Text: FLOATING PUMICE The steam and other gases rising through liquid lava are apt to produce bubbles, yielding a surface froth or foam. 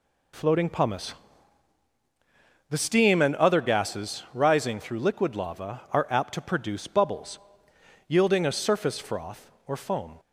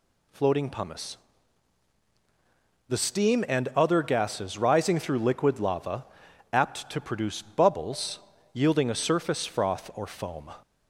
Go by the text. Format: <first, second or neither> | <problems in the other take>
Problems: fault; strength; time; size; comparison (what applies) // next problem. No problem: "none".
first | pauses between "PUMICE" and "The"; strong; at 1.1 s; 1.7 s long; strong in the first // skips "are"; at 6.2 s